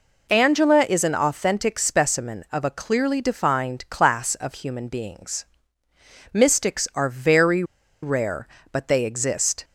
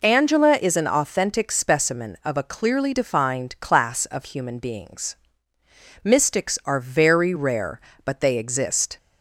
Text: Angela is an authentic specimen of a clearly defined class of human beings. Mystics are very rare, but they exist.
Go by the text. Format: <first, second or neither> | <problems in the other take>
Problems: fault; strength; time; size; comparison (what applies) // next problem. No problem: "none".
second | pauses between "very" and "rare"; at 7.6 s; 0.39 s long